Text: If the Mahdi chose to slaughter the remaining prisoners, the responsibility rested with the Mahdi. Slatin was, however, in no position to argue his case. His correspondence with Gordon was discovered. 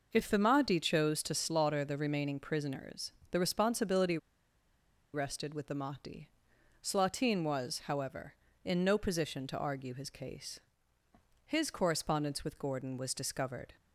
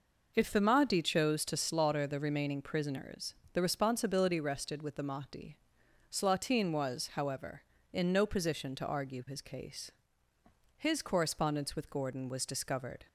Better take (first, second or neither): second